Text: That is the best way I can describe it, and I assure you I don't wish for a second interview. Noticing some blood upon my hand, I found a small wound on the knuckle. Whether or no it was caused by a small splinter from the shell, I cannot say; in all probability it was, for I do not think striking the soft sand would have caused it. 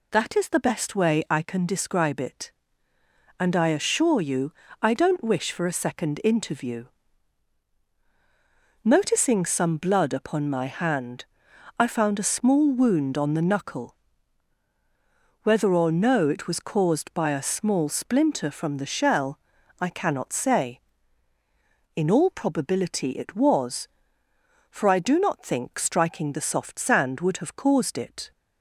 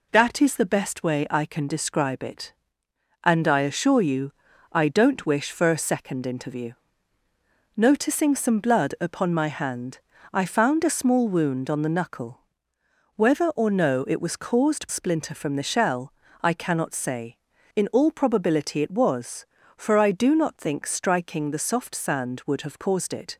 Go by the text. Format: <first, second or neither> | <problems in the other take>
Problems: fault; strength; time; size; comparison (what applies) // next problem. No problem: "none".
first | pauses between "you" and "I"; at 4.3 s; 0.40 s long; slight in the first // skips "by a small"; at 14.8 s